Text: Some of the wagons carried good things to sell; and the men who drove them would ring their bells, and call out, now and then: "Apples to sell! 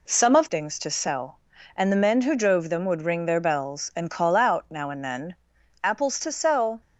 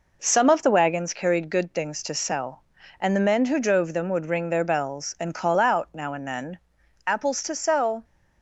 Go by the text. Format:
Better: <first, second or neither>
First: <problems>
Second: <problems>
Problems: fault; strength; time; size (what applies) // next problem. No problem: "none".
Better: second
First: skips "the wagons carried good"; at 0.4 s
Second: none